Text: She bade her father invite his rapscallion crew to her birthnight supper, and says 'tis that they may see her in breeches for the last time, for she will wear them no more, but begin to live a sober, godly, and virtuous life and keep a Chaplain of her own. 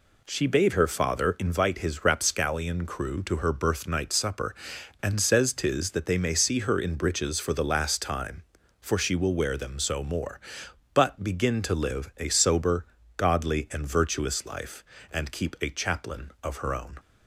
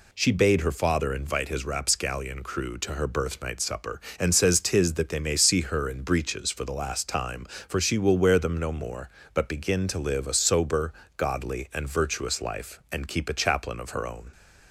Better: second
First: says "so" for "no"; at 9.7 s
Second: none

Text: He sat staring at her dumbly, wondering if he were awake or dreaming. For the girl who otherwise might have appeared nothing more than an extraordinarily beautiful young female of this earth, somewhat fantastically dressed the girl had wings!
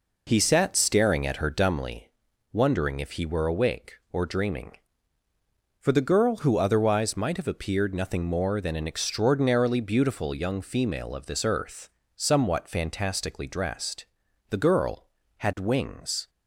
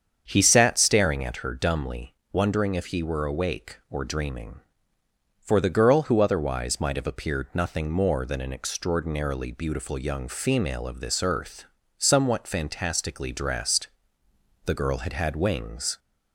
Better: first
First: pauses between "dressed" and "the"; noticeable; at 14.0 s; 0.46 s long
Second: starts louder than the rest; strong; until 1.2 s; 7.5 dB // pauses between "dressed" and "the"; noticeable; at 13.8 s; 0.78 s long // says "had" twice; at 15.1 s

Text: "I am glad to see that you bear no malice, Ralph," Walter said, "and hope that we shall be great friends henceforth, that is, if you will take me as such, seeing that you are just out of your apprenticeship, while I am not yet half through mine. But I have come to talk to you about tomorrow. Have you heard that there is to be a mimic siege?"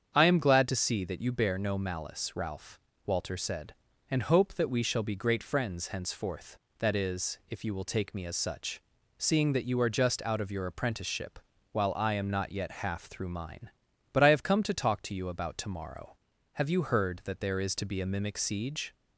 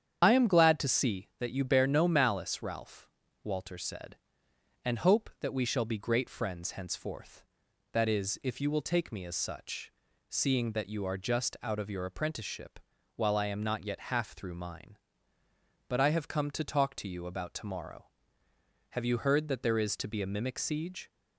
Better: first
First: starts louder than the rest; strong; until 1.1 s; 7.5 dB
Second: loses the start of "I"; at 0.2 s; 55 ms // starts louder than the rest; strong; until 1.2 s; 8.5 dB

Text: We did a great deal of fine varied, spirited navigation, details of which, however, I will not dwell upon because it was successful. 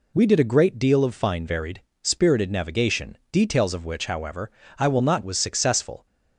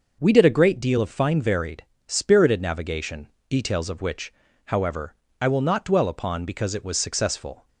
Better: second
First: skips "dwell upon because it"; at 5.2 s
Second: none

